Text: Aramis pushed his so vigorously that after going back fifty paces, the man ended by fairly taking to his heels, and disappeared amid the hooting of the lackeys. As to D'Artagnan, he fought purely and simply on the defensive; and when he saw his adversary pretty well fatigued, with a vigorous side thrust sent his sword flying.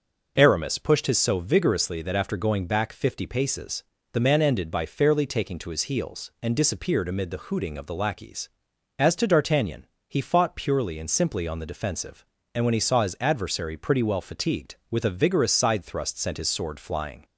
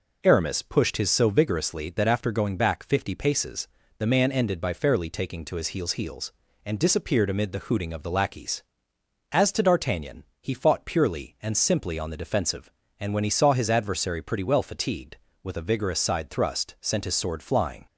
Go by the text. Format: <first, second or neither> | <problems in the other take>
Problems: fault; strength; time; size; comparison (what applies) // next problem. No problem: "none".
first | says "heels" twice; at 5.9 s